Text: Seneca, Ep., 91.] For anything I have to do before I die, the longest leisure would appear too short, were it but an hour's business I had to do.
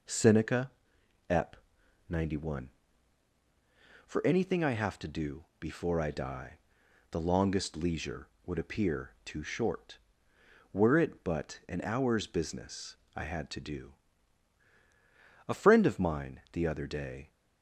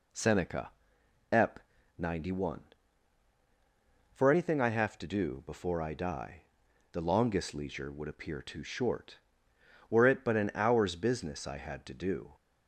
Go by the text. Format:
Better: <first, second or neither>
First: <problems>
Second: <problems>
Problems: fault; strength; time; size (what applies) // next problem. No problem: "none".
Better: second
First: pauses between "business" and "I"; slight; at 12.9 s; 0.20 s long // goes on to say "A friend of mine the other day"; strong; from 15.4 s on; 1.8 s long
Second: none